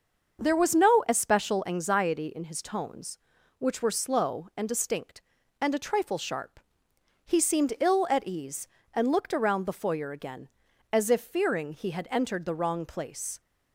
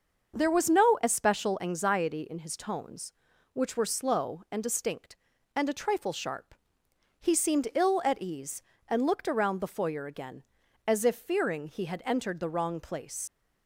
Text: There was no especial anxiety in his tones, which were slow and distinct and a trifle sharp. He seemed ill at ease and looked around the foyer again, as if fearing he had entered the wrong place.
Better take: first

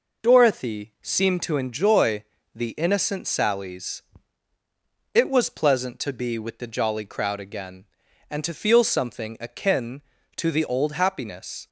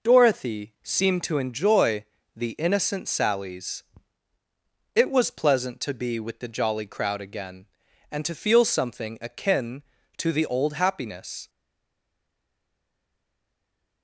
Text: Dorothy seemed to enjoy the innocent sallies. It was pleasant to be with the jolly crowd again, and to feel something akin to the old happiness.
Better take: first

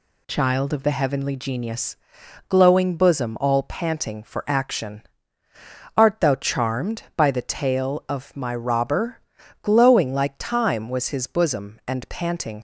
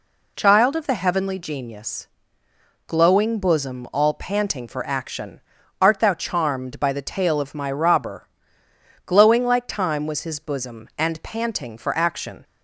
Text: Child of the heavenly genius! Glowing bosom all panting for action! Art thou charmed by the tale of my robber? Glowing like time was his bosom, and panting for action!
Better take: second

